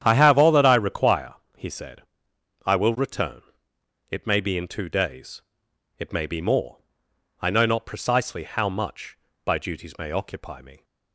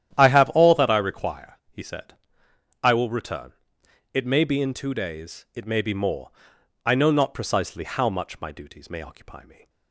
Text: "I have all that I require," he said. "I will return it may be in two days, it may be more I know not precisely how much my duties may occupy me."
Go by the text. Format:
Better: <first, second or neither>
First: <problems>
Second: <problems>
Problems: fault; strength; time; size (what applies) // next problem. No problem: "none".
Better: second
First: starts louder than the rest; strong; until 1.0 s; 9.5 dB // pauses between "return" and "it"; noticeable; at 3.4 s; 0.68 s long // pauses between "more" and "I"; noticeable; at 6.7 s; 0.64 s long // says "by" for "my"; at 9.4 s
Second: starts louder than the rest; strong; until 1.2 s; 10.5 dB // pauses between "return" and "it"; noticeable; at 3.5 s; 0.60 s long // pauses between "more" and "I"; noticeable; at 6.2 s; 0.54 s long